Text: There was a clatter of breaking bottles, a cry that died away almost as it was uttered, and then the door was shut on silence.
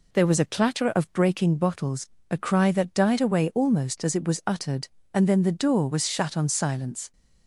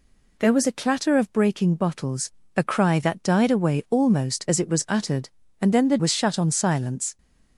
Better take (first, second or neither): first